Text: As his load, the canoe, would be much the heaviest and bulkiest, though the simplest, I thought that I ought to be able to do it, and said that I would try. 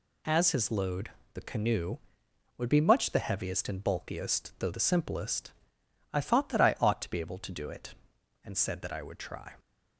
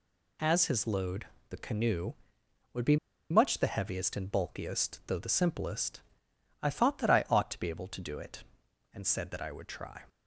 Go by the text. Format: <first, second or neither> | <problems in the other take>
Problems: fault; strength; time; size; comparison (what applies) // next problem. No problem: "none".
first | pauses between "be" and "much"; slight; at 2.9 s; 0.34 s long